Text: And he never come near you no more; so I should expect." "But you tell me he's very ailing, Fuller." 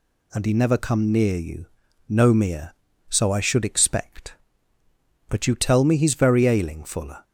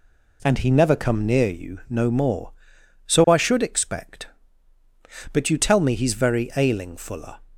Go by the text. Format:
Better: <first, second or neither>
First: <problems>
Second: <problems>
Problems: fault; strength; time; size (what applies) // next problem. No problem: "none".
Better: second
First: pauses between "you" and "no"; noticeable; at 1.6 s; 0.46 s long // says "mere" for "more"; at 2.3 s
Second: none